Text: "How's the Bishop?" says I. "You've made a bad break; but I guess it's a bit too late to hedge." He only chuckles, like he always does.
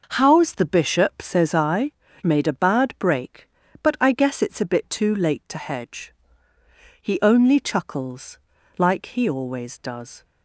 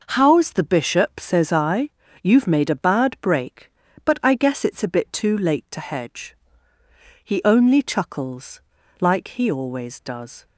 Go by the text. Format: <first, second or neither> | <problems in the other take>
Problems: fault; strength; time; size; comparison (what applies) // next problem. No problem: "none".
second | skips "You've"; at 2.0 s